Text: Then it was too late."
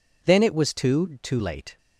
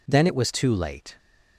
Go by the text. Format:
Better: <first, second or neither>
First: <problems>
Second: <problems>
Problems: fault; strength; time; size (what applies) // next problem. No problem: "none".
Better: second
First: says "too" twice; at 1.2 s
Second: none